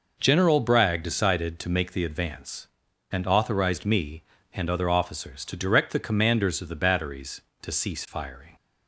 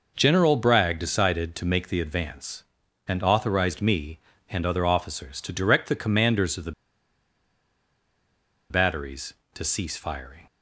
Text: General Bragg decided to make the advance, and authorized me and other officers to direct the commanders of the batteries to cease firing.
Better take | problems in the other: first | pauses between "the" and "batteries"; strong; at 6.7 s; 1.9 s long

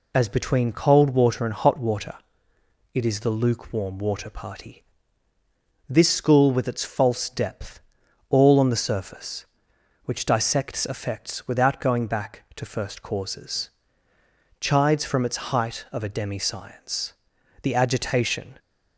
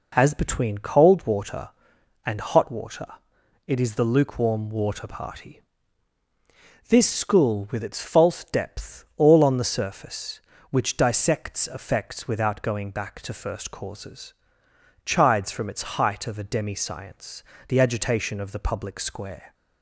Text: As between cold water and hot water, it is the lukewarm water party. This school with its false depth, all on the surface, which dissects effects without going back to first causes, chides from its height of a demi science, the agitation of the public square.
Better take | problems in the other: second | stops before "of the public square"; at 18.5 s

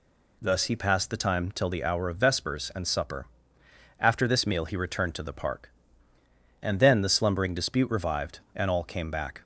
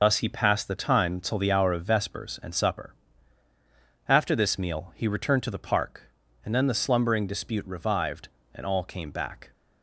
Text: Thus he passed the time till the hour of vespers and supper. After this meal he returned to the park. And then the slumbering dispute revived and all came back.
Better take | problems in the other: first | loses the start of "Thus"; at 0.0 s; 55 ms

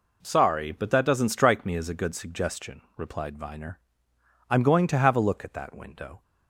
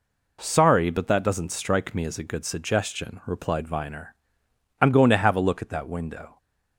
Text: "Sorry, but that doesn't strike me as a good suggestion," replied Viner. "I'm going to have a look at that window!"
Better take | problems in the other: neither | none

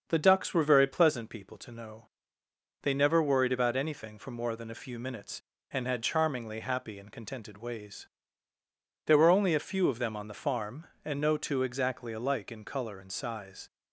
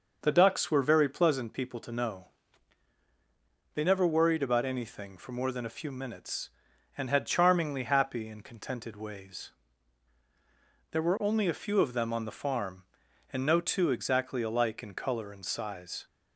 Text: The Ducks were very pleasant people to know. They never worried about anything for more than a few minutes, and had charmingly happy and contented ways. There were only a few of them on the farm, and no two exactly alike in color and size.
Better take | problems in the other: neither | starts louder than the rest; the same in both

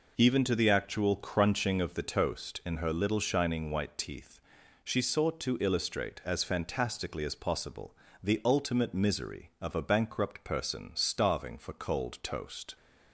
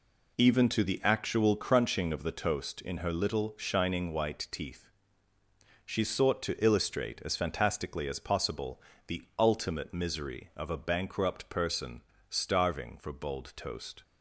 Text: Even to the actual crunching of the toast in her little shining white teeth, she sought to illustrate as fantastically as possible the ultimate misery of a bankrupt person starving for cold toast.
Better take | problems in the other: first | pauses between "possible" and "the"; slight; at 8.8 s; 0.26 s long; slight in the first // pauses between "person" and "starving"; slight; at 12.0 s; 0.28 s long // says "bold" for "cold"; at 13.1 s

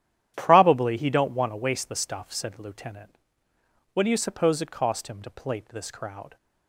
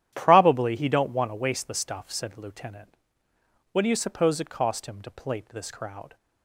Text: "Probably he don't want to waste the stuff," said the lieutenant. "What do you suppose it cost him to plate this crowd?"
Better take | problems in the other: neither | starts louder than the rest; strong; the same in both

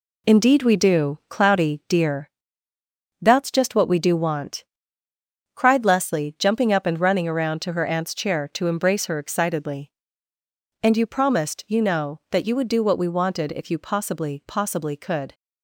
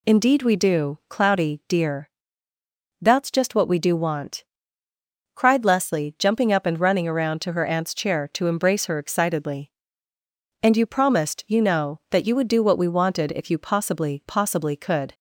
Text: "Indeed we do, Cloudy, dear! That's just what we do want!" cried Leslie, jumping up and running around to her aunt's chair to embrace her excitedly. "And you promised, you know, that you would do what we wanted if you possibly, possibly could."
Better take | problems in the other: second | gets quieter; throughout; 7 dB

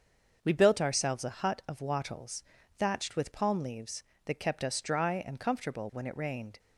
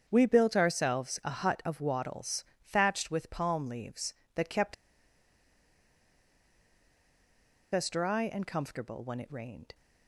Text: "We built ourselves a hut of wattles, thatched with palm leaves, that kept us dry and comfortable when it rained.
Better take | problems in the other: first | starts louder than the rest; strong; until 1.0 s; 7.5 dB; also in the first // pauses between "kept" and "us"; strong; at 4.7 s; 2.9 s long

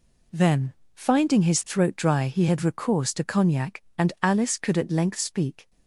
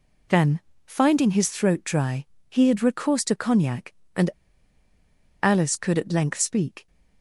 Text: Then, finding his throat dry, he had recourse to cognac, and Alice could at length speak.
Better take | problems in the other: first | pauses between "and" and "Alice"; at 4.2 s; 1.1 s long

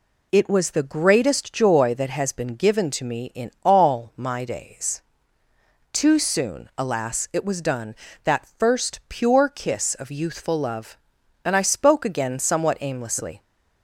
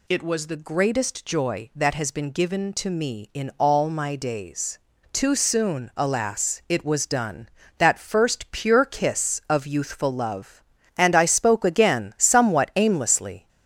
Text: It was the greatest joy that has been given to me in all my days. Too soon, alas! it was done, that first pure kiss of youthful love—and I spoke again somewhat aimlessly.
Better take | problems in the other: neither | none

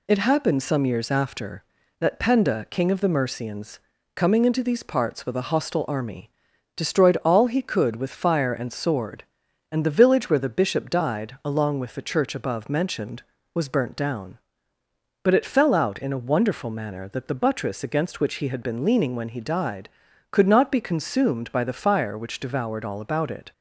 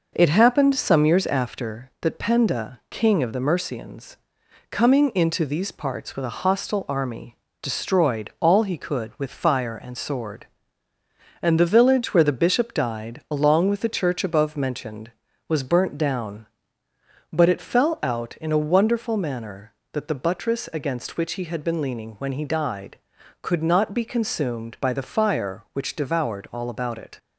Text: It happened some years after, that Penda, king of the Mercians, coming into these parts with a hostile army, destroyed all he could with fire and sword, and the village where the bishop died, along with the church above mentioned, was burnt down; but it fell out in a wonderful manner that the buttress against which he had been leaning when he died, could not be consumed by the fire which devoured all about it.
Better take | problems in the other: neither | none

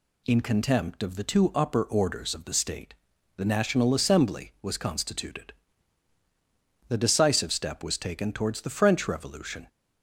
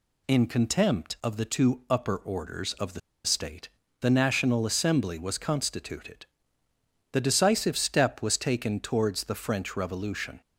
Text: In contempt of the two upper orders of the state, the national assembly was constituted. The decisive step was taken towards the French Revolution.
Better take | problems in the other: first | pauses between "the" and "state"; slight; at 2.9 s; 0.26 s long

